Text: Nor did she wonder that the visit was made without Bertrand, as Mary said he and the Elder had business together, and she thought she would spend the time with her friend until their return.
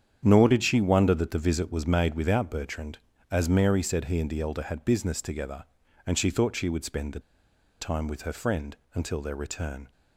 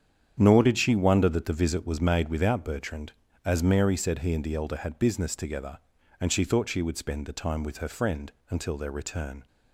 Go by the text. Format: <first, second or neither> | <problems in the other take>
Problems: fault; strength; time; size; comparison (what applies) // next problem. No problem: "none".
second | starts louder than the rest; strong; until 1.2 s; 8.5 dB; strong in the second // pauses between "the" and "time"; noticeable; at 7.1 s; 0.59 s long // pauses between "friend" and "until"; slight; at 8.7 s; 0.20 s long; slight in the second